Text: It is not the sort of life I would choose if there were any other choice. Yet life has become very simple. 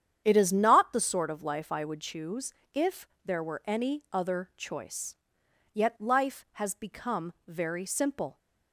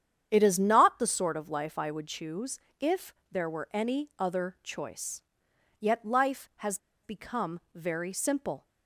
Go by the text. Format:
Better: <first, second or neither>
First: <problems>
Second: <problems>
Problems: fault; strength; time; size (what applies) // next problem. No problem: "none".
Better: first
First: starts louder than the rest; strong; until 1.2 s; 9 dB // pauses between "choose" and "if"; slight; at 2.5 s; 0.20 s long // pauses between "if" and "there"; slight; at 3.0 s; 0.16 s long // pauses between "become" and "very"; slight; at 7.3 s; 0.16 s long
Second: starts louder than the rest; strong; until 1.3 s; 9 dB // pauses between "choose" and "if"; slight; at 2.5 s; 0.20 s long // pauses between "if" and "there"; slight; at 3.1 s; 0.16 s long // pauses between "has" and "become"; slight; at 6.7 s; 0.25 s long // pauses between "become" and "very"; slight; at 7.5 s; 0.16 s long